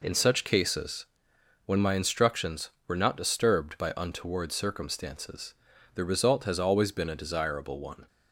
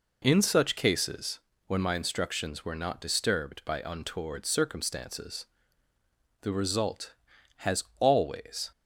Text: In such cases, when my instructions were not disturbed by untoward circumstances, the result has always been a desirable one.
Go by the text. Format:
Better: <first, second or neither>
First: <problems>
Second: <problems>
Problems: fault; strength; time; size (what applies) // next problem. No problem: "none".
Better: first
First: none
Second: pauses between "has" and "always"; slight; at 7.8 s; 0.16 s long // stops before "been a desirable one"; at 8.7 s